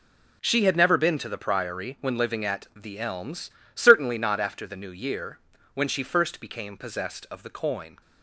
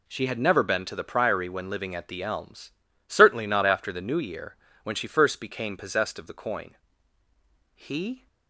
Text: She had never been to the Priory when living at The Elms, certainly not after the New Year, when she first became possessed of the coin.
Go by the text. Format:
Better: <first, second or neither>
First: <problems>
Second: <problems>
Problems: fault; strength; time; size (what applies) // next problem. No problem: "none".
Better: first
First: none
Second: goes on to say "He"; from 7.7 s on; 0.52 s long